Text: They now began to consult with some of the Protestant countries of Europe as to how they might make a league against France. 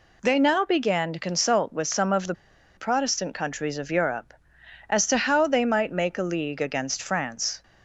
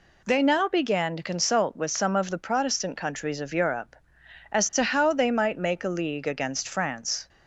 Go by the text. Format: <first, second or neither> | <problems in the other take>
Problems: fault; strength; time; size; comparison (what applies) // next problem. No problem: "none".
second | pauses between "the" and "Protestant"; at 2.3 s; 0.42 s long